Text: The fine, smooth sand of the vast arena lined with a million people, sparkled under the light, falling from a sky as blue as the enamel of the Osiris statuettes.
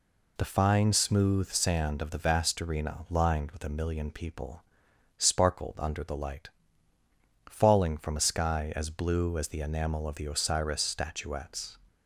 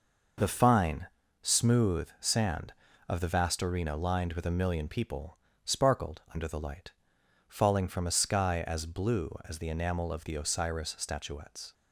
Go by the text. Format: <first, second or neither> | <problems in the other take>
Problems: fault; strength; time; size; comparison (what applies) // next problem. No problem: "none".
neither | none